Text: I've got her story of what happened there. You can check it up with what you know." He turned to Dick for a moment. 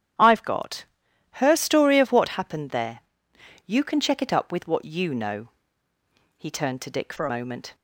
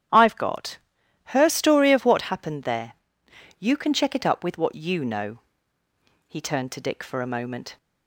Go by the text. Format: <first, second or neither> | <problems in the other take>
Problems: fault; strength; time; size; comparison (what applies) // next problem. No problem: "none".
second | starts louder than the rest; strong; until 1.7 s; 10.5 dB; strong in the second // pauses between "got" and "her"; noticeable; at 0.8 s; 0.52 s long; noticeable in the second // changes voice from "for" to "a"; from 7.1 to 7.2 s; 0.1 s long